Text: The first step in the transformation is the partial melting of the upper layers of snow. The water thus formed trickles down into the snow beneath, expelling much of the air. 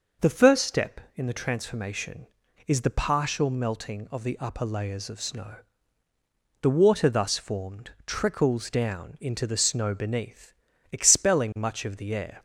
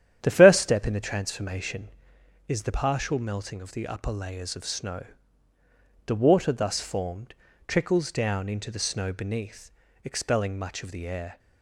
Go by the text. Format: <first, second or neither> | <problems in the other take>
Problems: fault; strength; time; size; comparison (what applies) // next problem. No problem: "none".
first | starts louder than the rest; strong; until 2.0 s; 10 dB // pauses between "formed" and "trickles"; slight; at 7.3 s; 0.34 s long